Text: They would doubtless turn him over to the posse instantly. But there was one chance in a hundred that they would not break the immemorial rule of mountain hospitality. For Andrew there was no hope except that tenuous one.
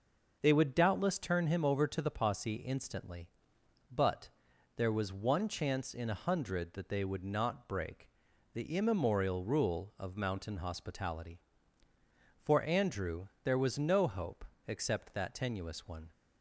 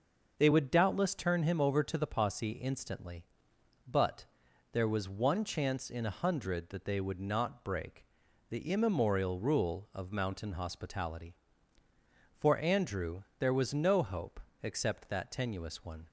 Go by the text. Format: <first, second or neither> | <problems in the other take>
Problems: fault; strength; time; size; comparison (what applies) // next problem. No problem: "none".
neither | pauses between "But" and "there"; noticeable; the same in both // pauses between "break" and "the"; the same in both // pauses between "Andrew" and "there"; slight; the same in both // pauses between "hope" and "except"; slight; the same in both